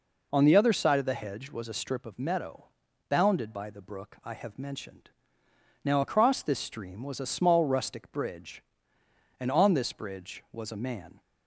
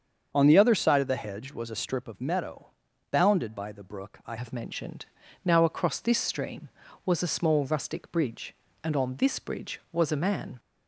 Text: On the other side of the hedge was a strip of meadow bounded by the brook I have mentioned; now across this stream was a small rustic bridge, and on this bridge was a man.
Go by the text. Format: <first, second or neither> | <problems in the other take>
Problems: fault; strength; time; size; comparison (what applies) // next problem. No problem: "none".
first | starts louder than the rest; strong; until 1.3 s; 7 dB // pauses between "meadow" and "bounded"; at 2.6 s; 0.42 s long; also in the first // changes voice at "have"; from 4.3 s on; 6.2 s long